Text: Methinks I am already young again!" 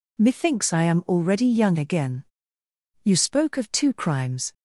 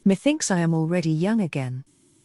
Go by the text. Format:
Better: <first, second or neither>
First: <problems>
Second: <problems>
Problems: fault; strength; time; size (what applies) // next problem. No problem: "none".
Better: second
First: goes on to say "You spoke of two crimes"; from 3.0 s on; 1.5 s long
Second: none